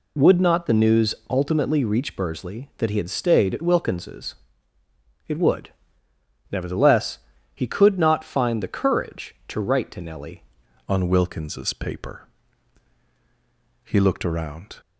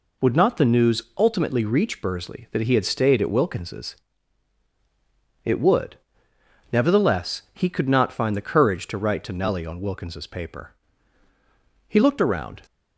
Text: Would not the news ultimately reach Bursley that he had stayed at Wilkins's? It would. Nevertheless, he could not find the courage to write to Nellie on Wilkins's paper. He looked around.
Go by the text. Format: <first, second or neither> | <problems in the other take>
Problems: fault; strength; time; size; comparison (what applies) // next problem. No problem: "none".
second | pauses between "news" and "ultimately"; slight; at 1.1 s; 0.16 s long; slight in the second // changes voice at "on"; from 10.8 s on; 4.0 s long